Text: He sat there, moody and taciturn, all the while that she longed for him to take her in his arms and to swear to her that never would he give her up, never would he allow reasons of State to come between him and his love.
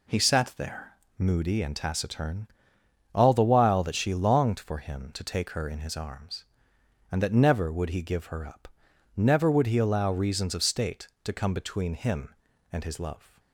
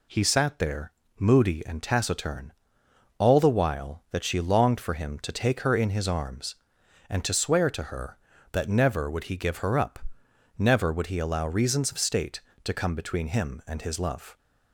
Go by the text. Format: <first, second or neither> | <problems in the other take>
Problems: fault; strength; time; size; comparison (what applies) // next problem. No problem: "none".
second | skips "to swear to her"; at 7.2 s